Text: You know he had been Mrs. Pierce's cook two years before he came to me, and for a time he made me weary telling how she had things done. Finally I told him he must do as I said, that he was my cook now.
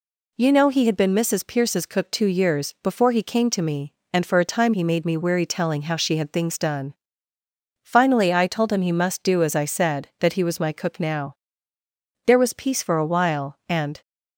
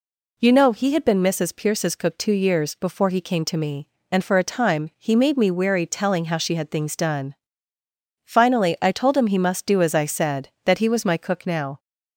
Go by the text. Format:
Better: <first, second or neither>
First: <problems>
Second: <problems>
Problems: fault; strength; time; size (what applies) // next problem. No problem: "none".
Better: second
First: goes on to say "There was peace for a while and"; strong; from 12.2 s on; 1.7 s long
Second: none